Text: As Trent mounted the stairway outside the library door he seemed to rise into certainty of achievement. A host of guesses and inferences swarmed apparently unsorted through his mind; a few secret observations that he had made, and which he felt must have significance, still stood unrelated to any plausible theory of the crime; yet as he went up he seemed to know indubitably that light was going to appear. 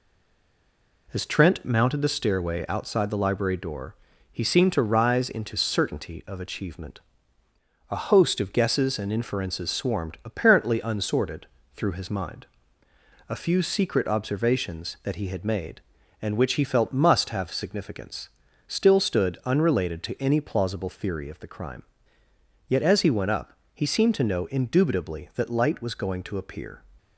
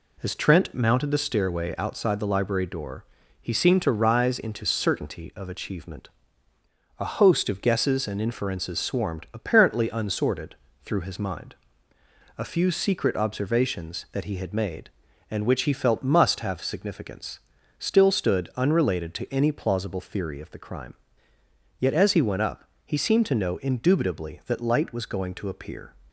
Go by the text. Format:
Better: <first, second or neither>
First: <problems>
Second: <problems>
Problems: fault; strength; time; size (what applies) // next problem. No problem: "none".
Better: second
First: stays silent before the first word; until 1.0 s; 1.0 s long // pauses between "door" and "he"; slight; at 3.9 s; 0.36 s long // pauses between "unsorted" and "through"; slight; at 11.4 s; 0.28 s long // pauses between "up" and "he"; slight; at 23.5 s; 0.20 s long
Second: pauses between "door" and "he"; slight; at 3.0 s; 0.36 s long // pauses between "unsorted" and "through"; slight; at 10.5 s; 0.28 s long // pauses between "up" and "he"; slight; at 22.6 s; 0.20 s long